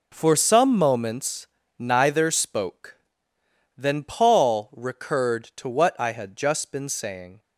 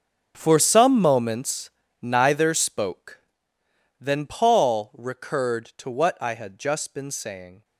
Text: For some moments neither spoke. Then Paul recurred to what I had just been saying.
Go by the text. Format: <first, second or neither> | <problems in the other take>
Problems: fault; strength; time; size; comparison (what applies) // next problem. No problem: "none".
first | gets quieter; strong; throughout; 15.5 dB // pauses between "moments" and "neither"; slight; at 1.6 s; 0.32 s long; slight in the first